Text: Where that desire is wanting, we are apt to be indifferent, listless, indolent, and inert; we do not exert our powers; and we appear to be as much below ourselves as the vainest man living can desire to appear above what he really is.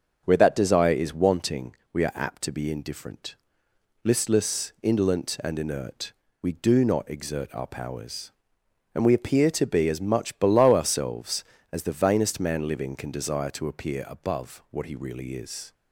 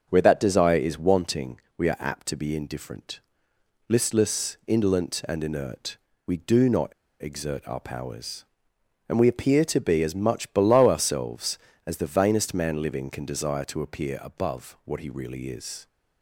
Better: first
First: starts louder than the rest; until 1.2 s; 6.5 dB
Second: starts louder than the rest; until 1.1 s; 6.5 dB // pauses between "not" and "exert"; slight; at 6.9 s; 0.30 s long

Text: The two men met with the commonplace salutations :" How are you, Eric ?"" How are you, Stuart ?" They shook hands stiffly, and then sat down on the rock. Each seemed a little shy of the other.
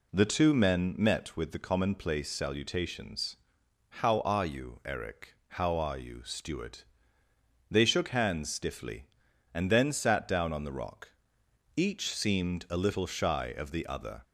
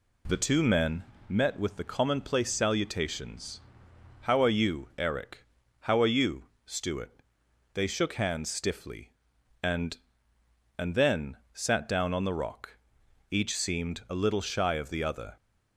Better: first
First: none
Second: pauses between "men" and "met"; slight; at 1.0 s; 0.24 s long // says "and" twice; at 10.7 s // pauses between "then" and "sat"; slight; at 11.3 s; 0.18 s long

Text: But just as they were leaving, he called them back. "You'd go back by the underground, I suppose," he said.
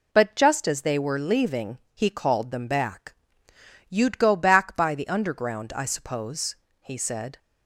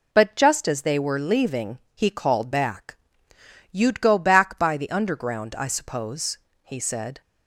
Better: first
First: none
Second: skips "them"; at 2.5 s

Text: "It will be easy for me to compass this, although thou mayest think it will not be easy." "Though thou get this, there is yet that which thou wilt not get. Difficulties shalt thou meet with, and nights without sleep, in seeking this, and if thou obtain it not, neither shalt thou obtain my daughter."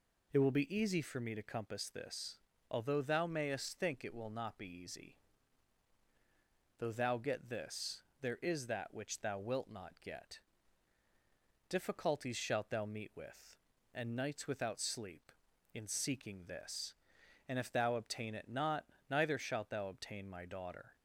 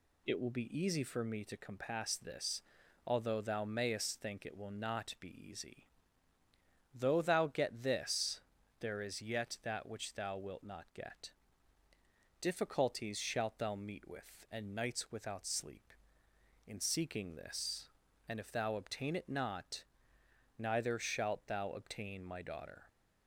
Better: second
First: skips "yet"; at 8.6 s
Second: none

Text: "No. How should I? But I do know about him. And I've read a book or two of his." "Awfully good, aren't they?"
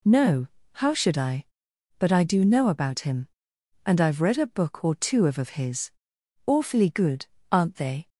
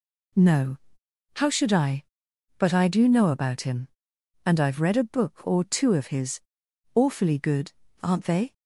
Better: second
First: says "of" twice; at 5.3 s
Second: none

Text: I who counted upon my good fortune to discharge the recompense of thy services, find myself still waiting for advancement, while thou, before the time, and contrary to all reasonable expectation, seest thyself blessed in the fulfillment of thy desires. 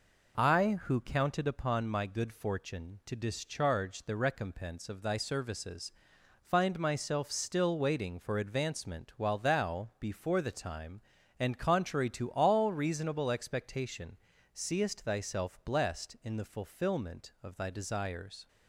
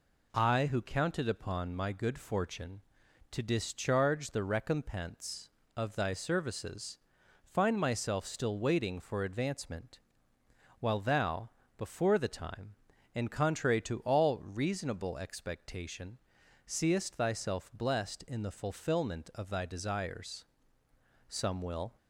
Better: first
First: none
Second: goes on to say "Some will"; noticeable; from 21.2 s on; 0.68 s long

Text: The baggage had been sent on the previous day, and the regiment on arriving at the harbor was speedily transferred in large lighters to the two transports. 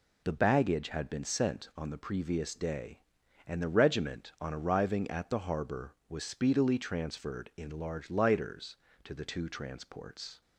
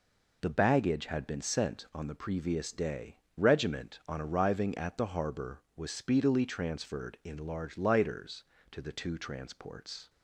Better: first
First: none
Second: skips "and the"; at 3.2 s

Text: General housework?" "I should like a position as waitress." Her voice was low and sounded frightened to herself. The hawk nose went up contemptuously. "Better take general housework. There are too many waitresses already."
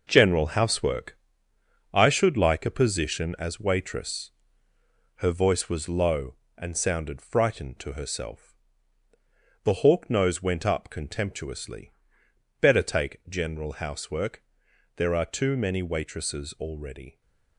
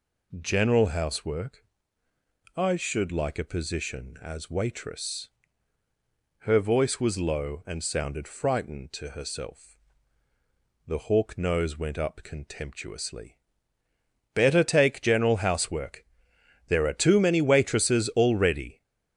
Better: second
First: gets quieter; strong; throughout; 8.5 dB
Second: none

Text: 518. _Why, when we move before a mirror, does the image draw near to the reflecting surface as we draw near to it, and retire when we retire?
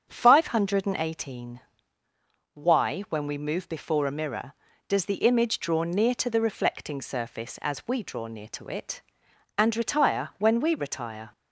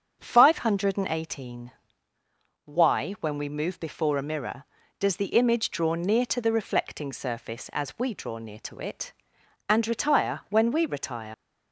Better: first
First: starts louder than the rest; until 1.2 s; 7 dB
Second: starts louder than the rest; until 1.3 s; 7 dB // leaves "retire" unfinished; at 11.3 s; 90 ms

